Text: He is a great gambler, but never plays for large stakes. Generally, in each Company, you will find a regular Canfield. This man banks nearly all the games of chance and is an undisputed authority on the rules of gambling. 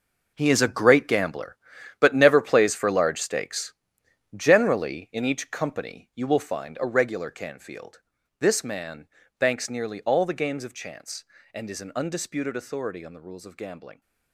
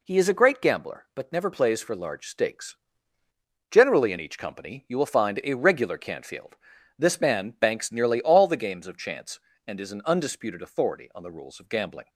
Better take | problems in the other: second | gets quieter; strong; throughout; 12.5 dB // pauses between "man" and "banks"; slight; at 9.0 s; 0.30 s long

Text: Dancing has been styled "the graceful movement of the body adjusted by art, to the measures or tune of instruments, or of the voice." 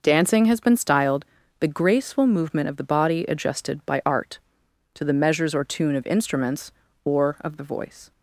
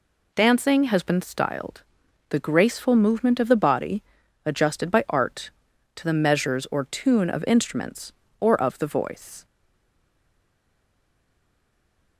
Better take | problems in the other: first | pauses between "styled" and "the"; noticeable; at 1.8 s; 0.48 s long; slight in the first // pauses between "body" and "adjusted"; at 4.0 s; 0.44 s long // stays silent after the last word; strong; from 9.4 s on; 2.7 s long

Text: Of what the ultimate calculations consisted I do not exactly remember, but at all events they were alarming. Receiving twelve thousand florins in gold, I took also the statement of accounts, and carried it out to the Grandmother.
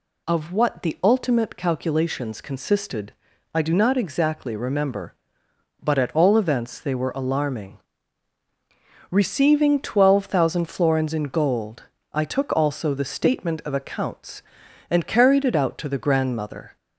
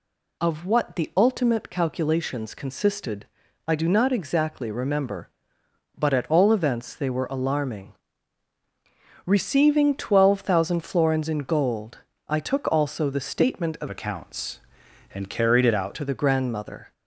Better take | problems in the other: first | pauses between "consisted" and "I"; at 3.2 s; 0.40 s long; also in the first // changes voice from "accounts" to "out"; from 13.9 to 15.9 s; 2.0 s long

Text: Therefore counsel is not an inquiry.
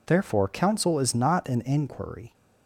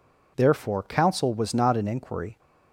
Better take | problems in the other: first | says "was" for "is"; at 1.3 s

